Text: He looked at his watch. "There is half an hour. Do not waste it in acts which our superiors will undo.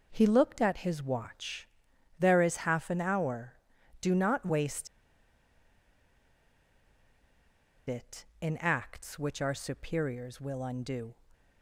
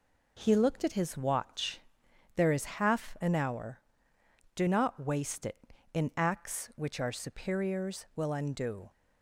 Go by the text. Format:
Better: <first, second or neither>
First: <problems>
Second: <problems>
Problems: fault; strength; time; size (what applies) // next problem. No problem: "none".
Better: second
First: pauses between "waste" and "it"; strong; at 4.8 s; 3.0 s long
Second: none